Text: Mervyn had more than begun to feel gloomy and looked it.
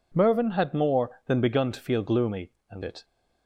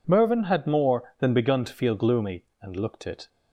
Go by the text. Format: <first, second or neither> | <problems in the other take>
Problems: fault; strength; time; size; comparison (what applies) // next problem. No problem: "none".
second | skips "looked"; at 2.8 s